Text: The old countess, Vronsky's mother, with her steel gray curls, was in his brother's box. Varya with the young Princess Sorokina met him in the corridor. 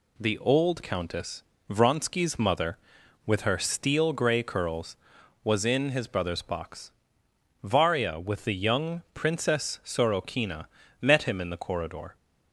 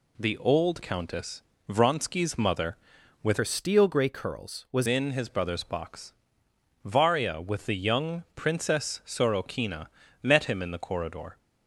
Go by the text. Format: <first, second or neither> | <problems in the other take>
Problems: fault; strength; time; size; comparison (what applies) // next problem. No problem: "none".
first | changes voice from "her" to "was"; from 3.3 to 4.8 s; 1.5 s long // pauses between "Sorokina" and "met"; slight; at 9.8 s; 0.34 s long; slight in the first